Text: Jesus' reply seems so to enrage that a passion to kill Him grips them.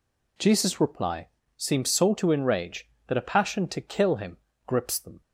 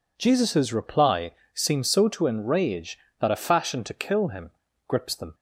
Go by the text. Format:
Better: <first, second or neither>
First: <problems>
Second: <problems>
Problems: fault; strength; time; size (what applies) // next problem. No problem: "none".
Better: first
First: pauses between "reply" and "seems"; slight; at 1.2 s; 0.28 s long // pauses between "Him" and "grips"; slight; at 4.3 s; 0.30 s long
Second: pauses between "reply" and "seems"; slight; at 1.3 s; 0.23 s long // says "fashion" for "passion"; at 3.3 s // pauses between "Him" and "grips"; slight; at 4.5 s; 0.34 s long